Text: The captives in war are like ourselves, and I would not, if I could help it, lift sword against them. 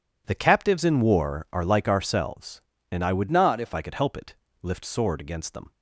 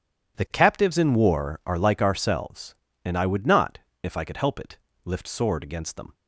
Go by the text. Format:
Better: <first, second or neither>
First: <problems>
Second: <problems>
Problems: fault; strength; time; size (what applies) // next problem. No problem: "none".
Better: second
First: changes voice from "not" to "if"; from 3.3 to 3.7 s; 0.4 s long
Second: none